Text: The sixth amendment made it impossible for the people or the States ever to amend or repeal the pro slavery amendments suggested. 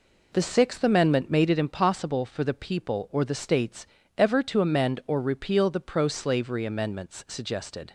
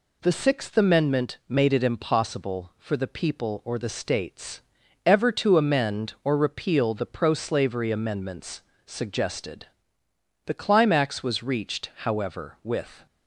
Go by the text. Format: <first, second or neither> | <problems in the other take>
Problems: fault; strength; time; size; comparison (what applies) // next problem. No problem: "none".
first | pauses between "States" and "ever"; noticeable; at 4.5 s; 0.46 s long; slight in the first // pauses between "amendments" and "suggested"; slight; at 8.6 s; 0.24 s long // goes on to say "The climax was reached however with"; strong; from 10.4 s on; 2.6 s long